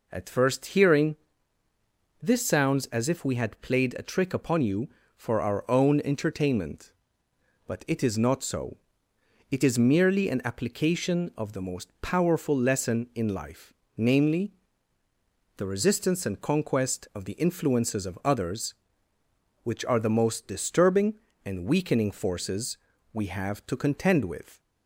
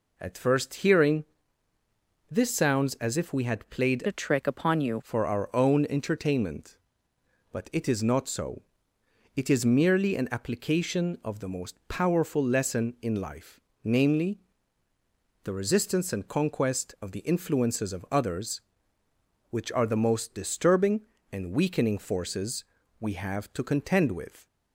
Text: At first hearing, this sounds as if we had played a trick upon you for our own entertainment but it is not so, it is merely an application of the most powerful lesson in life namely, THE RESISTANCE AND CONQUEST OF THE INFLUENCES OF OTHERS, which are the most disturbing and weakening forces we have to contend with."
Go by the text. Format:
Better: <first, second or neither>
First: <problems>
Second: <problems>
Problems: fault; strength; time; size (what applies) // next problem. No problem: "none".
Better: first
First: pauses between "life" and "namely"; slight; at 13.7 s; 0.26 s long // pauses between "forces" and "we"; at 22.7 s; 0.38 s long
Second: changes voice from "a" to "you"; from 4.0 to 5.0 s; 1.0 s long // pauses between "life" and "namely"; slight; at 13.5 s; 0.26 s long // pauses between "forces" and "we"; at 22.6 s; 0.38 s long